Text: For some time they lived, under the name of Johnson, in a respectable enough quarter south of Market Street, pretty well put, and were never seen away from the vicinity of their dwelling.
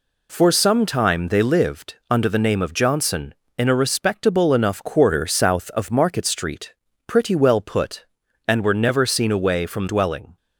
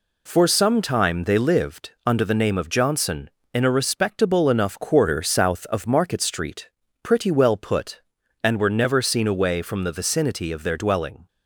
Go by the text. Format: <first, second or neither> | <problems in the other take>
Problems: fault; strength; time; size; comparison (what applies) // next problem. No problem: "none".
second | skips "the vicinity of their"; at 9.8 s